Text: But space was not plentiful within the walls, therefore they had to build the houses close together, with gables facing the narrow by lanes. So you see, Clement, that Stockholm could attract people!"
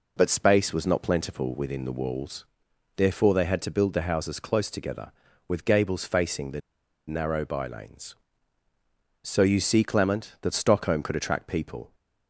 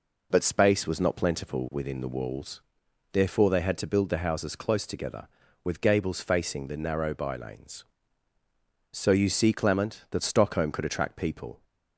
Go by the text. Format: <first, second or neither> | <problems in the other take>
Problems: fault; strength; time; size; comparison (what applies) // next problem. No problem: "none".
second | pauses between "the" and "narrow"; noticeable; at 6.5 s; 0.48 s long